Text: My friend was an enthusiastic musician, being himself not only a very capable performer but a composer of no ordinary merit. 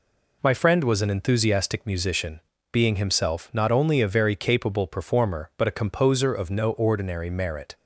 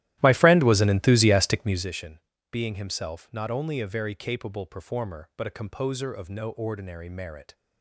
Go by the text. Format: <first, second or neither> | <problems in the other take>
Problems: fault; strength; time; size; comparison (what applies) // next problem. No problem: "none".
first | starts louder than the rest; strong; until 1.9 s; 14.5 dB